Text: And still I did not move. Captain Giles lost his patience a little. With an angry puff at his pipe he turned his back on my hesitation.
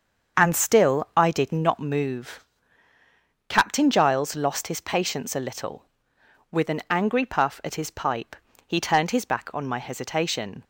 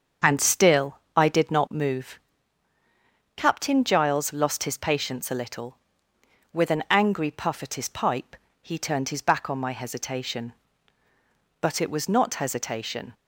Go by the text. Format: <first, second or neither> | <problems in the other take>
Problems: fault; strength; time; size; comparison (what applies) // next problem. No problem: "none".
first | starts louder than the rest; strong; until 1.4 s; 7 dB; also in the first // pauses between "still" and "I"; slight; at 0.9 s; 0.18 s long // pauses between "pipe" and "he"; slight; at 8.3 s; 0.26 s long; slight in the first // goes on to say "But it was not hesitation"; from 11.6 s on; 1.5 s long